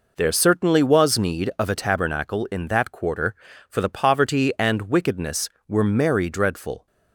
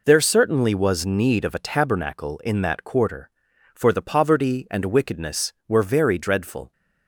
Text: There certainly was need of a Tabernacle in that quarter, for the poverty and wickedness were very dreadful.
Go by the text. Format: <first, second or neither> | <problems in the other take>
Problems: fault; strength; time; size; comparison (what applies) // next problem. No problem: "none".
second | says "merry" for "very"; at 5.8 s